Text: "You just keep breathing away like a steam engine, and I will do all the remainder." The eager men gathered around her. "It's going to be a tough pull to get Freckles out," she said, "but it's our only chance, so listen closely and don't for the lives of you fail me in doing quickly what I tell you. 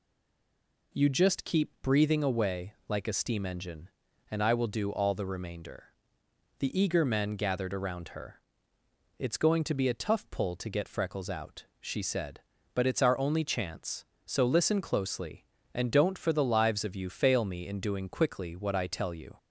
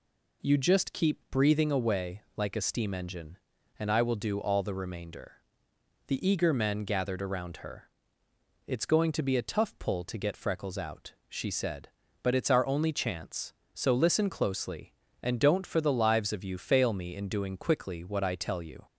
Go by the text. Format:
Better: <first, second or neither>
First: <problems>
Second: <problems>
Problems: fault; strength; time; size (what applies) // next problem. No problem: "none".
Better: second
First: stays silent before the first word; slight; until 0.9 s; 0.9 s long // pauses between "away" and "like"; slight; at 2.7 s; 0.16 s long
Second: pauses between "away" and "like"; slight; at 2.2 s; 0.16 s long